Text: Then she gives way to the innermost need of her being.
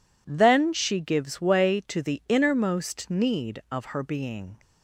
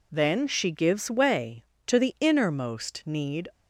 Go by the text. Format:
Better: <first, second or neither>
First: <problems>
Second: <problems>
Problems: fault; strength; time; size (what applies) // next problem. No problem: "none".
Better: first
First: none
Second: stops before "of her being"; at 3.5 s